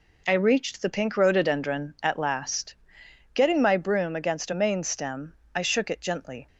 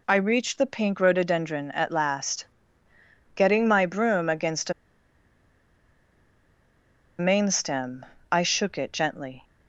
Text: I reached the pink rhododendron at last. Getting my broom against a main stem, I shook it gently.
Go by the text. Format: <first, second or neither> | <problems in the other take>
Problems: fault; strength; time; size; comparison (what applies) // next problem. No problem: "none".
first | pauses between "a" and "main"; strong; at 4.7 s; 2.4 s long